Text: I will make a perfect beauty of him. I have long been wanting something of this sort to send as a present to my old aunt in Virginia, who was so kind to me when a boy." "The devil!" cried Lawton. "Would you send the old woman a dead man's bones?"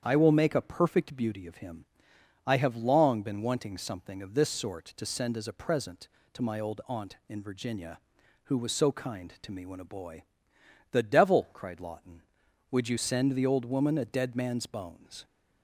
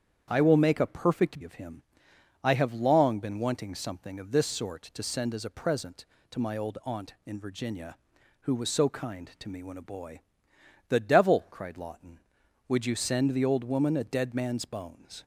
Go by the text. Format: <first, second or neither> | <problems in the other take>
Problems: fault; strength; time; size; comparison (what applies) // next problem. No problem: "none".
first | starts louder than the rest; strong; until 1.2 s; 8.5 dB; strong in the first // skips "beauty"; at 1.4 s